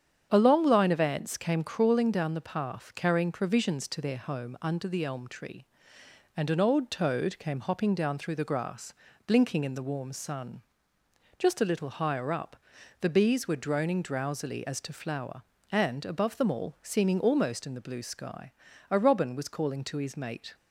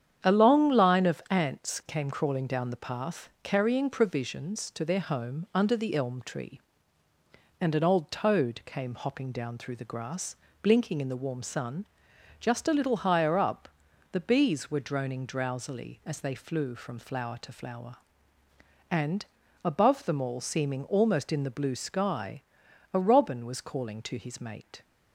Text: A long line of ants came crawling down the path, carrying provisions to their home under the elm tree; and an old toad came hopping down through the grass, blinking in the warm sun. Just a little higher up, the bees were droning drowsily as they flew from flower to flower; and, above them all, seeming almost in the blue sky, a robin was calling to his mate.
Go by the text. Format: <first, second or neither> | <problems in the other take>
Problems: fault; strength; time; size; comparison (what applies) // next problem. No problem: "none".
second | starts louder than the rest; strong; until 1.3 s; 8 dB; strong in the second // skips "they flew from flower"; at 14.7 s